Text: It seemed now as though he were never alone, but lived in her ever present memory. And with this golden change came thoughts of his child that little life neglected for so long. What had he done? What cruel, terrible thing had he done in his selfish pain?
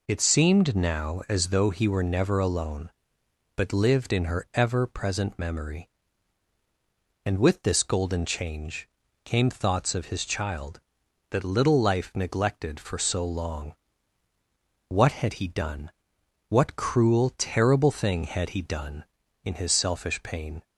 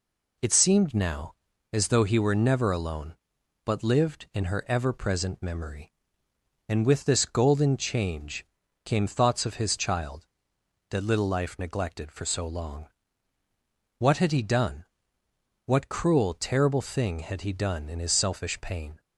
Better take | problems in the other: neither | pauses between "change" and "came"; the same in both

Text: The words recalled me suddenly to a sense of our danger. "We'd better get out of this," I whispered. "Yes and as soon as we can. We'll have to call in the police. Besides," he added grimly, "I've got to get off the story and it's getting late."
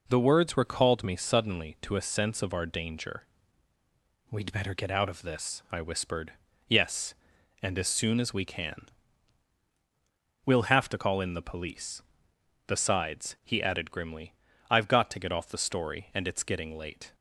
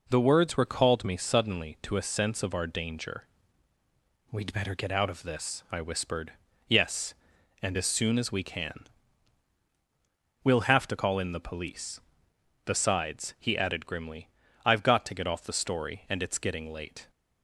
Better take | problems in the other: neither | none

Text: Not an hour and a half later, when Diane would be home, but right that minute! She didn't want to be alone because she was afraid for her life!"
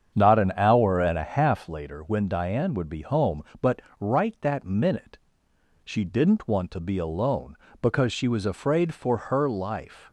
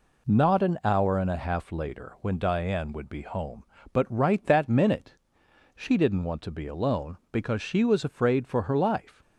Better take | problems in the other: second | starts louder than the rest; strong; until 1.8 s; 7.5 dB // pauses between "but" and "right"; slight; at 3.8 s; 0.20 s long

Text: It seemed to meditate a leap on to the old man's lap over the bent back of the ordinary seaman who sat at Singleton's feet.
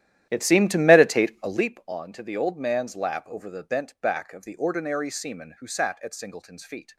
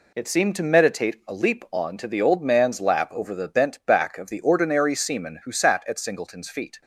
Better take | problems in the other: second | starts louder than the rest; strong; until 1.7 s; 12 dB

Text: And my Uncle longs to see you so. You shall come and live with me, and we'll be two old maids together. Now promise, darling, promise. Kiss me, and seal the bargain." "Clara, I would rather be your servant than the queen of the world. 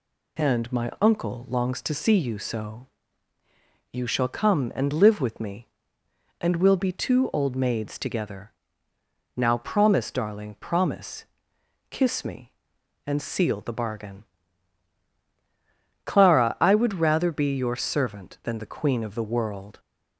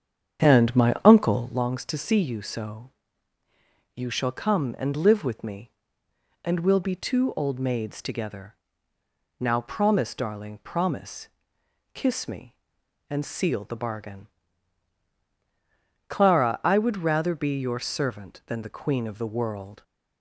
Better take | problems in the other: first | starts louder than the rest; strong; until 1.7 s; 8 dB

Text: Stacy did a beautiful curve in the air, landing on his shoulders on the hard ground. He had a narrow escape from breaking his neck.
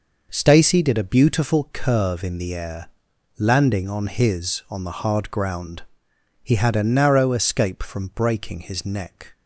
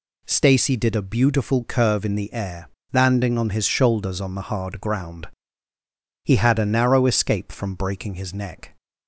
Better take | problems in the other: second | skips "shoulders"; at 4.6 s

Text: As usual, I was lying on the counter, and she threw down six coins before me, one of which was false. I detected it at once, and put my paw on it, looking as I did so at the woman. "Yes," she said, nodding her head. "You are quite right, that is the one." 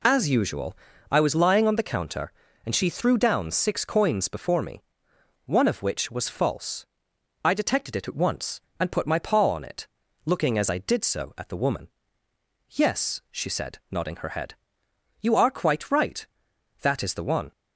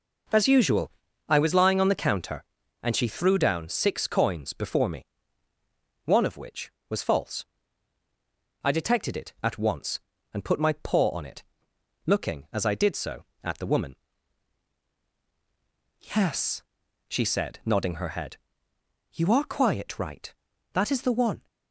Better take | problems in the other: first | says "quiet" for "quite"; at 19.5 s

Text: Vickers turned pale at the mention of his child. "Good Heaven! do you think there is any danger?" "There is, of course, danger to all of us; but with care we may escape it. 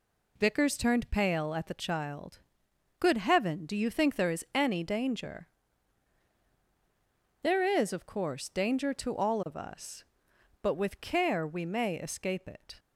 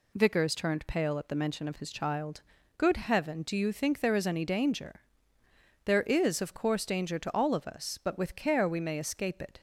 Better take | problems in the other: second | skips "mention of his"; at 1.7 s

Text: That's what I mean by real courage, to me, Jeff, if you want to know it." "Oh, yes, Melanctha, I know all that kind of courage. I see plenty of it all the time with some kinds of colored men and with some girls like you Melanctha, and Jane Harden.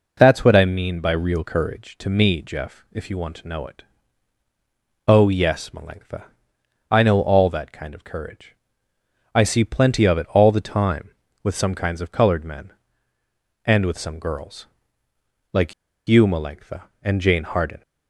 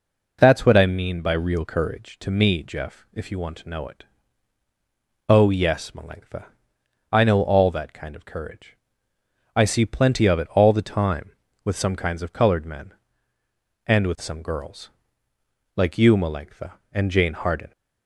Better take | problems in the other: second | pauses between "girls" and "like"; noticeable; at 14.6 s; 0.86 s long; noticeable in the second // pauses between "like" and "you"; at 15.7 s; 0.36 s long

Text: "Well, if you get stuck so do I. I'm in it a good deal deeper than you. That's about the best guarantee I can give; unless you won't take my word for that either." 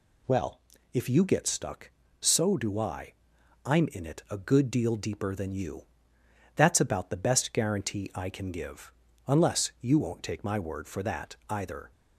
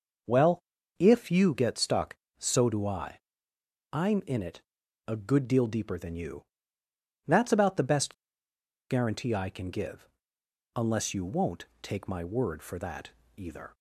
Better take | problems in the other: first | pauses between "it" and "a"; noticeable; at 4.6 s; 0.46 s long // pauses between "best" and "guarantee"; noticeable; at 8.1 s; 0.76 s long // pauses between "won't" and "take"; slight; at 11.6 s; 0.16 s long // pauses between "that" and "either"; slight; at 13.0 s; 0.26 s long

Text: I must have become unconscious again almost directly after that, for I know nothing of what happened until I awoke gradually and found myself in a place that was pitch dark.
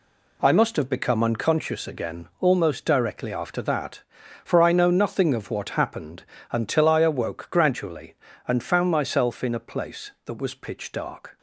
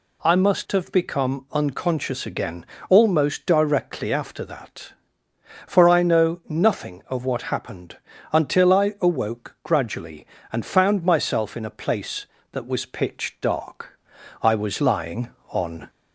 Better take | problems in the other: first | pauses between "again" and "almost"; slight; at 2.6 s; 0.22 s long // pauses between "happened" and "until"; slight; at 7.9 s; 0.34 s long; slight in the first // goes on to say "I was lying on"; from 14.4 s on; 1.4 s long

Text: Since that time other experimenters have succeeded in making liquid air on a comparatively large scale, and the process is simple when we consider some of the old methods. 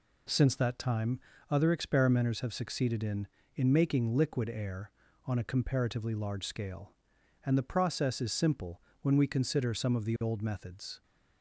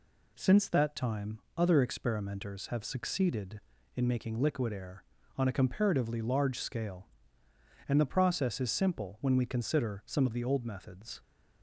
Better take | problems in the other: second | pauses between "time" and "other"; slight; at 1.1 s; 0.30 s long; slight in the second // says "in" twice; at 3.5 s // pauses between "simple" and "when"; slight; at 8.8 s; 0.18 s long

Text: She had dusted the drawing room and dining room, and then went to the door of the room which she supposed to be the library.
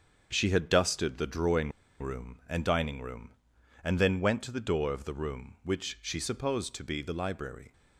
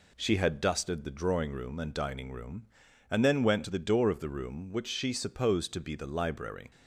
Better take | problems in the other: second | starts louder than the rest; until 1.3 s; 6.5 dB // pauses between "drawing" and "room"; slight; at 1.7 s; 0.30 s long

